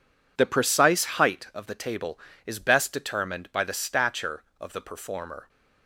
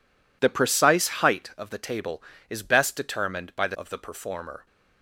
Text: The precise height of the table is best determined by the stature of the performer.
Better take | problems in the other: first | skips "stature"; at 3.7 s

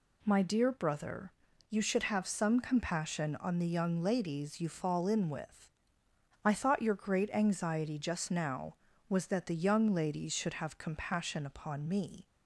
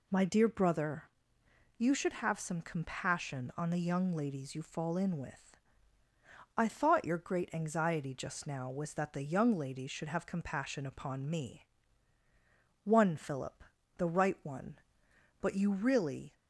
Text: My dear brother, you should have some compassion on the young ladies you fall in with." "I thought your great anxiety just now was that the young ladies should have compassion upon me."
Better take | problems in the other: first | goes on to say "One Philip the right one But you really"; strong; from 12.8 s on; 3.5 s long

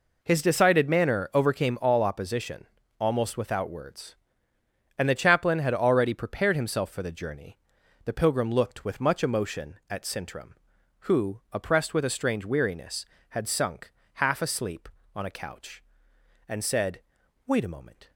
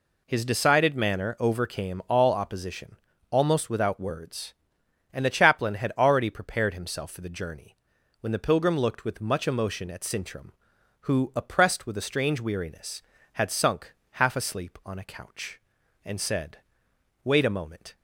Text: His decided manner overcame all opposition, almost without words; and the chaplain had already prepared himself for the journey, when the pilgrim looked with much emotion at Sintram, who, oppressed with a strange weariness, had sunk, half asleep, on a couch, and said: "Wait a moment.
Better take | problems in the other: second | skips "when"; at 7.8 s

